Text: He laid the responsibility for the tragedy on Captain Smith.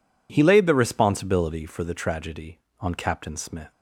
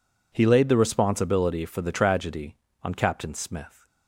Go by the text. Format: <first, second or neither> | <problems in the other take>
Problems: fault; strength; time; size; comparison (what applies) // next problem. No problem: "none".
neither | none